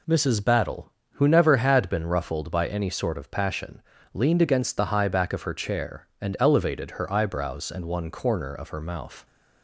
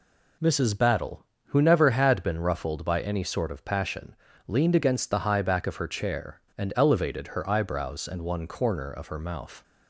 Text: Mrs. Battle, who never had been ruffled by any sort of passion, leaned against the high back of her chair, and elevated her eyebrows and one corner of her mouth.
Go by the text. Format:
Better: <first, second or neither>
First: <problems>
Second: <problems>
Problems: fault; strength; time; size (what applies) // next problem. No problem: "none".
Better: neither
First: none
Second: none